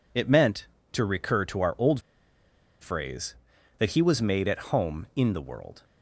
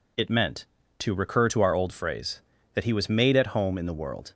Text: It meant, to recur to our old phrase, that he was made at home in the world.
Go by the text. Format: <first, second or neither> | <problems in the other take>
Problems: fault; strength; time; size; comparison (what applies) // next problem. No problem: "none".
second | pauses between "old" and "phrase"; noticeable; at 2.0 s; 0.80 s long